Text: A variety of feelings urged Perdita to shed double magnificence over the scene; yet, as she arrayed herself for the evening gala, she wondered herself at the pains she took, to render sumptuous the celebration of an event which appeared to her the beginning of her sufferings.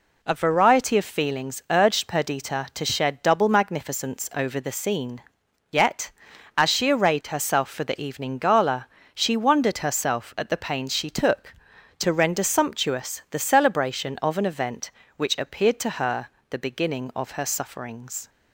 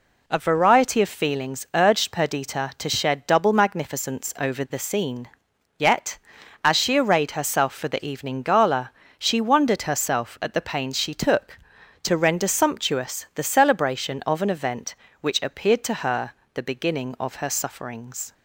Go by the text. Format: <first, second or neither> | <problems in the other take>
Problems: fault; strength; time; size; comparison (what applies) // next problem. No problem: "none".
neither | pauses between "her" and "the"; slight; the same in both